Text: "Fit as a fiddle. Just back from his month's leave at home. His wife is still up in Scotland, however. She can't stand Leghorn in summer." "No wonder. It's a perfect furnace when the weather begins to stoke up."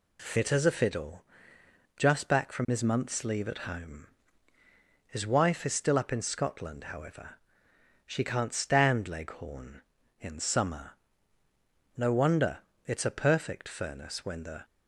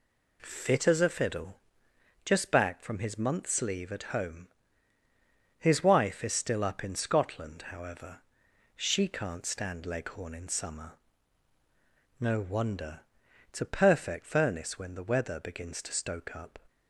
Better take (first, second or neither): second